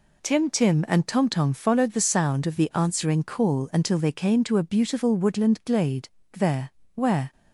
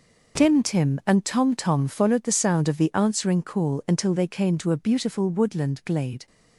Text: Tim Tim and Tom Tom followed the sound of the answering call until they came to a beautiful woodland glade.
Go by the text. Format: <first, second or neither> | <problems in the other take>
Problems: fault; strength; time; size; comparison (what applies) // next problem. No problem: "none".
second | goes on to say "There where"; noticeable; from 6.3 s on; 0.98 s long